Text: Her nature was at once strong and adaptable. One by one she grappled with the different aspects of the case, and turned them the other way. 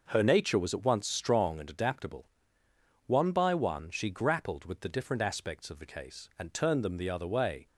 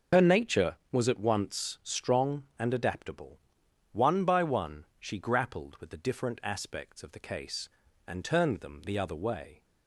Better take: first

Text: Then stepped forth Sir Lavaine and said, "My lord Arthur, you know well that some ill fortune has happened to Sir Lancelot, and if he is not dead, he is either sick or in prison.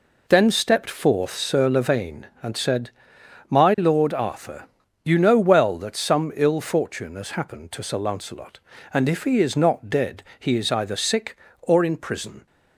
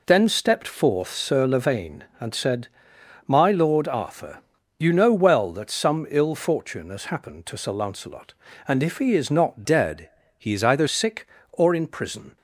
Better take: first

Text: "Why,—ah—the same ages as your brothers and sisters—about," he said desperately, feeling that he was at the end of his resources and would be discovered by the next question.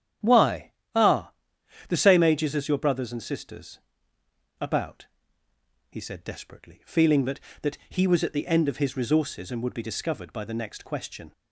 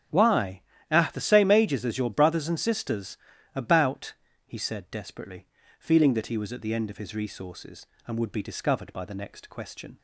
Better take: second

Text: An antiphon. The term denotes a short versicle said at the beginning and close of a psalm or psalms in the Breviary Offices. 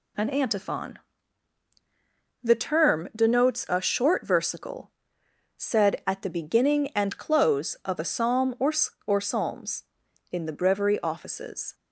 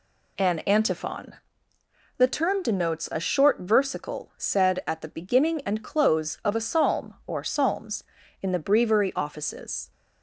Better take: second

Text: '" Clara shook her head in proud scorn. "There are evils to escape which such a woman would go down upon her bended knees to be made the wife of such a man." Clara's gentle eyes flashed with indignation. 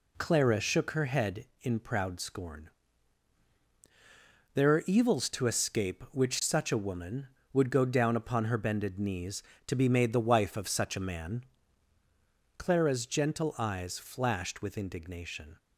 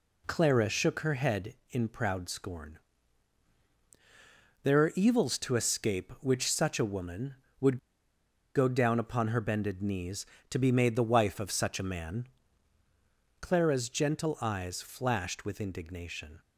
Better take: first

